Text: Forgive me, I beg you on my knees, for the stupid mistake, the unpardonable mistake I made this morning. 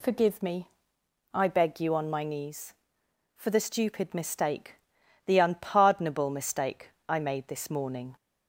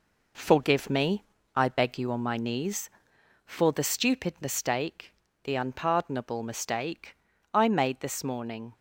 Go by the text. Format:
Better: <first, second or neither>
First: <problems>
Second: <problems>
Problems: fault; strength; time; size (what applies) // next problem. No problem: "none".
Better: first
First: pauses between "mistake" and "I"; slight; at 6.8 s; 0.18 s long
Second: gets quieter; noticeable; throughout; 6 dB // pauses between "mistake" and "I"; at 7.1 s; 0.38 s long